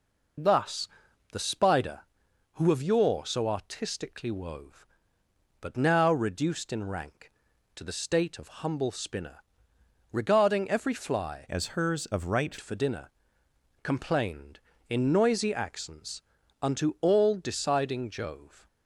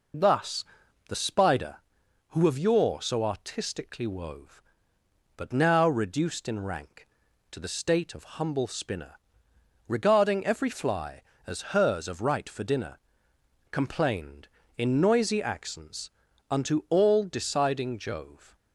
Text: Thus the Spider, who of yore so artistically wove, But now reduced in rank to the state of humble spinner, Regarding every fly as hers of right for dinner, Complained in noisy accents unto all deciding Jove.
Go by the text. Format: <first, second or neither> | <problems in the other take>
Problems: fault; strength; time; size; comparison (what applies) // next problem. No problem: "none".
second | pauses between "Thus" and "the"; noticeable; at 0.8 s; 0.46 s long; noticeable in the second // changes voice from "as" to "right"; from 11.5 to 12.5 s; 1.0 s long // pauses between "accents" and "unto"; at 16.2 s; 0.40 s long; also in the second